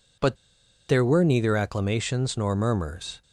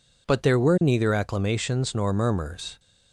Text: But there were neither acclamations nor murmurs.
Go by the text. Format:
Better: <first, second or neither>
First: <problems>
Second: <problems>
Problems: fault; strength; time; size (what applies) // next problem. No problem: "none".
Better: second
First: pauses between "But" and "there"; noticeable; at 0.3 s; 0.52 s long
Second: none